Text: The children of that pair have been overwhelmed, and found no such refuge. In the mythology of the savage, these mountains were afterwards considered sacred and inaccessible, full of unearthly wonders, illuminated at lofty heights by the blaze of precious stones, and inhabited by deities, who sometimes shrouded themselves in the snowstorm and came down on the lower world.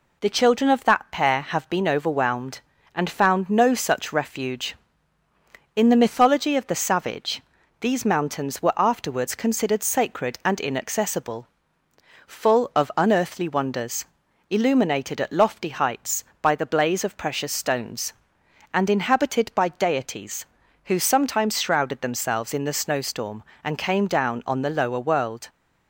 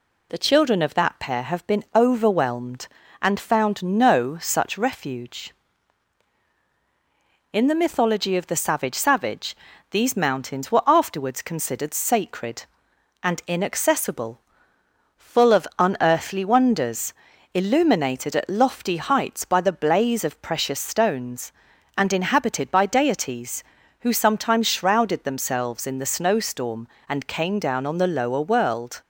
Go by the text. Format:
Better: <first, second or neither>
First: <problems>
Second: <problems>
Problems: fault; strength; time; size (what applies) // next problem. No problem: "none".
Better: first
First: none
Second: says "savage" twice; at 8.9 s